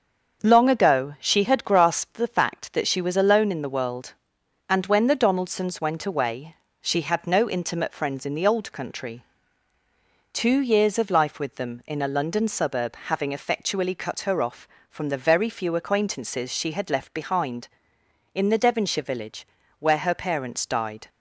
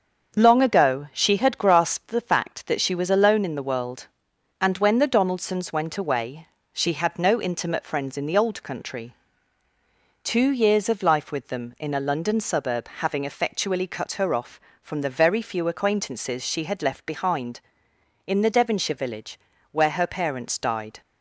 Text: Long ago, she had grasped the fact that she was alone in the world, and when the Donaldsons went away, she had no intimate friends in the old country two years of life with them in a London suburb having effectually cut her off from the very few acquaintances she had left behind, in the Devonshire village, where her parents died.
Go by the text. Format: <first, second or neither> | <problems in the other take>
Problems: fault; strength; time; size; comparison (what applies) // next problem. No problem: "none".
neither | starts louder than the rest; the same in both // pauses between "country" and "two"; the same in both